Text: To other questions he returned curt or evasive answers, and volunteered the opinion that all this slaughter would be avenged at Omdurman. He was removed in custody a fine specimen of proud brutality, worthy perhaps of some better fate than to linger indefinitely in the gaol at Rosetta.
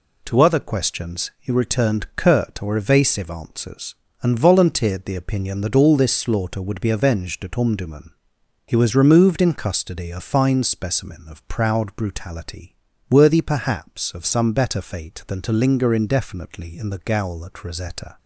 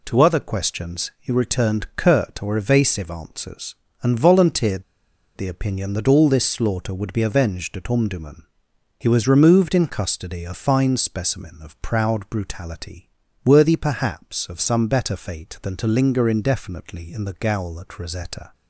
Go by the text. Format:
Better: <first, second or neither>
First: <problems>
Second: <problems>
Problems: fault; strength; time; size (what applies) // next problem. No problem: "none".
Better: first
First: none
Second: pauses between "volunteered" and "the"; noticeable; at 4.8 s; 0.53 s long